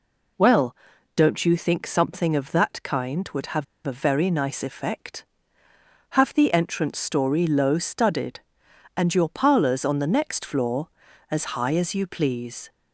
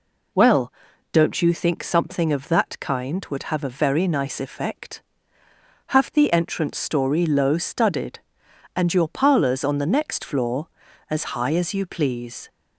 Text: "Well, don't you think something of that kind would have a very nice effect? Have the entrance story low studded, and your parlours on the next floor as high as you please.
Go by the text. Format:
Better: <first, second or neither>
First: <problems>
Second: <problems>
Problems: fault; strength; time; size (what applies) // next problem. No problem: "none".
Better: second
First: pauses between "have" and "a"; slight; at 3.6 s; 0.22 s long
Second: none